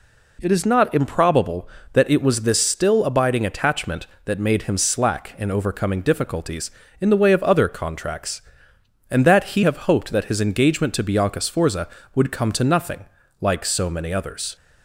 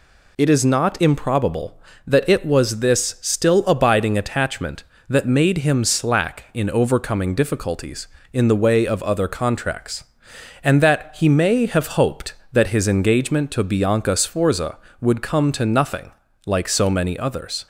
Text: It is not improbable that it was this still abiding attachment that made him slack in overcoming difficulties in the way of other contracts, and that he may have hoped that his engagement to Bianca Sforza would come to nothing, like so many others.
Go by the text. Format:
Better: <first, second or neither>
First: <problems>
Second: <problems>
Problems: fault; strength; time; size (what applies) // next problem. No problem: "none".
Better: second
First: skips "may"; at 9.6 s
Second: none